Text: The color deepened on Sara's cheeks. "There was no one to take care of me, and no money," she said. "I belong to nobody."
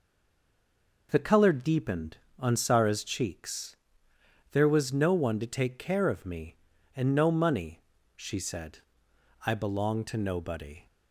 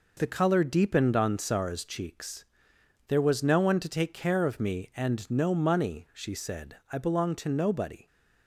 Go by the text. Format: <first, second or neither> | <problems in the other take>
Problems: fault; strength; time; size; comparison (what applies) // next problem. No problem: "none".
second | stays silent before the first word; until 1.0 s; 1.0 s long